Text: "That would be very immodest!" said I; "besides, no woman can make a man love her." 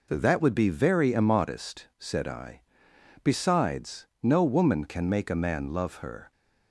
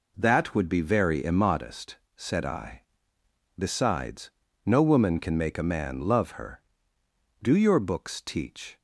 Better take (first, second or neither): first